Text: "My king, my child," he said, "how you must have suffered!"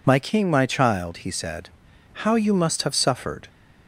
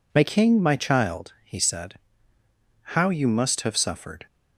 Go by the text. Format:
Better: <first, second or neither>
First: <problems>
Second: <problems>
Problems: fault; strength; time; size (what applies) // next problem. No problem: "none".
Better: neither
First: none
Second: none